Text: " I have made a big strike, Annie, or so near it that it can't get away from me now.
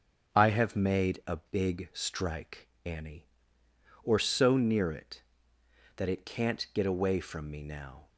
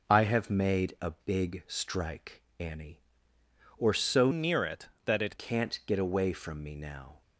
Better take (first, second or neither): first